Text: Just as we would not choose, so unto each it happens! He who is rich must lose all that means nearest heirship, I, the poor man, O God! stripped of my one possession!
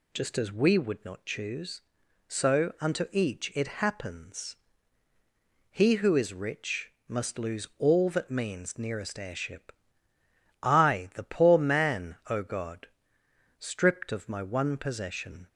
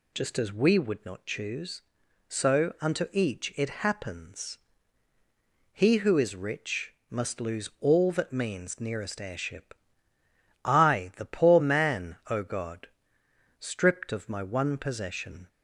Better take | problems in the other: neither | pauses between "rich" and "must"; slight; the same in both

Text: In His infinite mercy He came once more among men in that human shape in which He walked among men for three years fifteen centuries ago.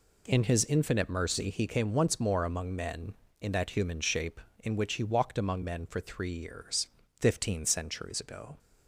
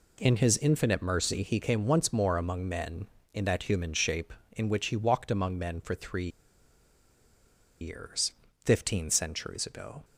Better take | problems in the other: first | pauses between "three" and "years"; strong; at 6.2 s; 1.5 s long // pauses between "years" and "fifteen"; slight; at 8.3 s; 0.34 s long; slight in the first

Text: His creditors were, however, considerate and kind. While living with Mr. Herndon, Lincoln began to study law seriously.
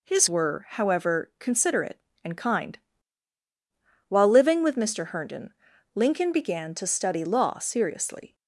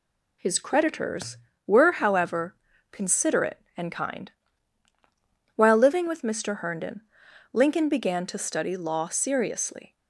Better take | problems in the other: second | skips "creditors"; at 0.2 s

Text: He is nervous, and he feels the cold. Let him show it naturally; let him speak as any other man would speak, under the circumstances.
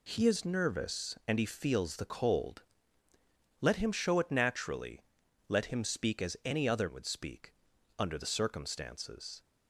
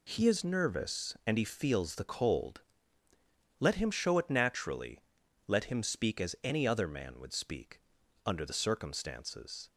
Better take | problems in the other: second | skips "man"; at 6.8 s

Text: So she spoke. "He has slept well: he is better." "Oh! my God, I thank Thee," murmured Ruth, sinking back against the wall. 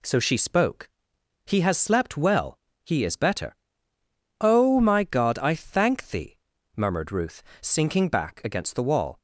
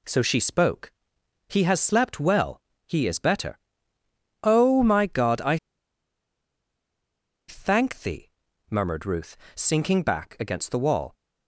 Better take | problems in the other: first | pauses between "I" and "thank"; strong; at 5.5 s; 1.9 s long

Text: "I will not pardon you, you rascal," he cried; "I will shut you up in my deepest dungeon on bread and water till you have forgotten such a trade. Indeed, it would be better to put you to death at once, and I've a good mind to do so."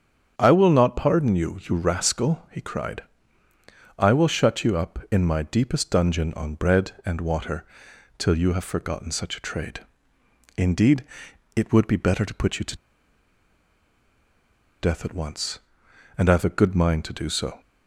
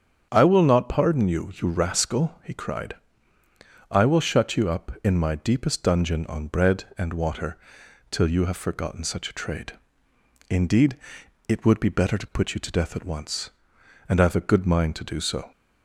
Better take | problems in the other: second | starts louder than the rest; strong; until 1.3 s; 8 dB; strong in the second // pauses between "water" and "till"; noticeable; at 7.6 s; 0.54 s long; noticeable in the second // pauses between "to" and "death"; strong; at 12.7 s; 2.0 s long

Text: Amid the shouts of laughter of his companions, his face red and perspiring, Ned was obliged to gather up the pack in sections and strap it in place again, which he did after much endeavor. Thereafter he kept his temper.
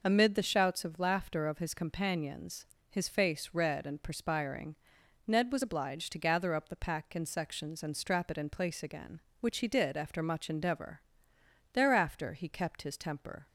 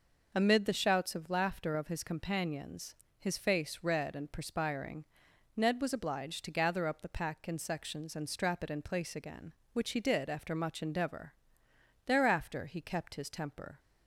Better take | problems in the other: neither | none

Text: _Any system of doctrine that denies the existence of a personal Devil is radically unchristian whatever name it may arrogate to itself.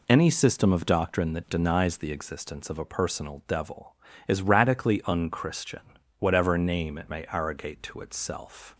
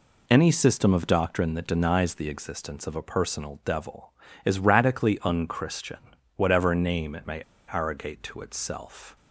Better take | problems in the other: first | pauses between "unchristian" and "whatever"; at 5.9 s; 0.38 s long; also in the first // pauses between "may" and "arrogate"; slight; at 7.4 s; 0.27 s long

